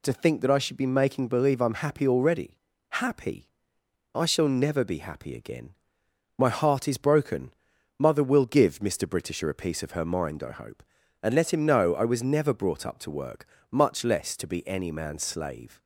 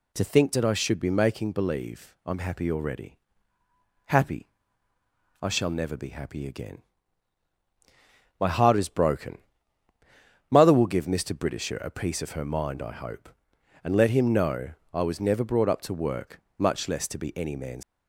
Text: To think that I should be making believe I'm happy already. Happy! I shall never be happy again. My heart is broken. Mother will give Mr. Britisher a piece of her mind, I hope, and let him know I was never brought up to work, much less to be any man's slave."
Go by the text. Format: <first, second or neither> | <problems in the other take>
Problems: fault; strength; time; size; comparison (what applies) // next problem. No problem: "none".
first | pauses between "know" and "I"; slight; at 14.6 s; 0.22 s long // stops before "slave"; at 17.8 s